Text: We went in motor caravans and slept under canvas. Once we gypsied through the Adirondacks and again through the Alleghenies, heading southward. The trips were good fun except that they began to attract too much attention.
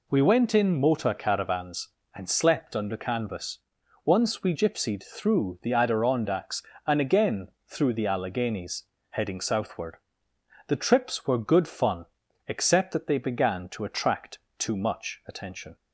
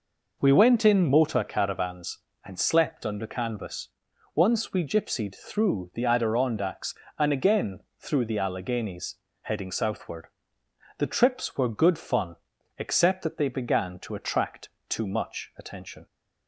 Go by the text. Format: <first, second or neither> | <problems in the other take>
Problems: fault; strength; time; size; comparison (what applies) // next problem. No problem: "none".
first | starts louder than the rest; noticeable; until 1.5 s; 5 dB // pauses between "again" and "through"; slight; at 7.7 s; 0.20 s long; slight in the first // pauses between "fun" and "except"; at 12.3 s; 0.42 s long; also in the first // pauses between "attract" and "too"; slight; at 14.6 s; 0.22 s long; slight in the first